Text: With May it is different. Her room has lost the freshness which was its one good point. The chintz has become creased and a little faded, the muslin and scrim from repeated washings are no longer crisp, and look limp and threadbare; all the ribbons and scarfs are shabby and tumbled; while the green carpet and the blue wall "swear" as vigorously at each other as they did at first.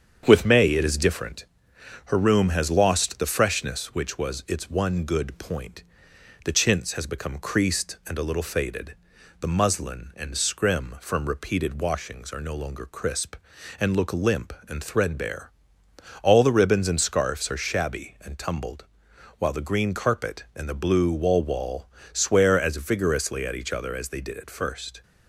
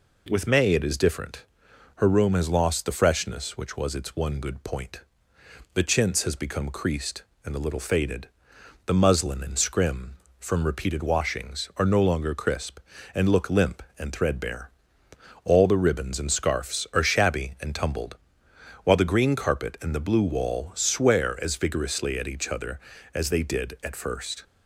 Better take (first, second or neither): second